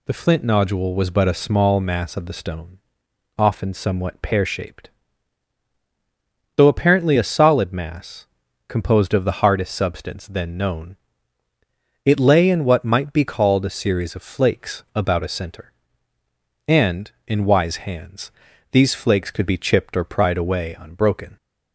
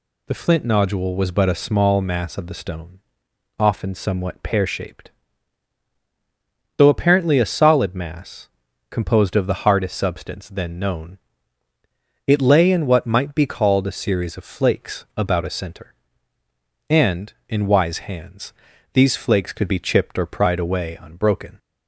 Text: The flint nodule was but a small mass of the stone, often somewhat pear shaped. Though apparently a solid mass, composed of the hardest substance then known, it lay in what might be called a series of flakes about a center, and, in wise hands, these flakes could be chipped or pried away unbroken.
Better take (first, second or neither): neither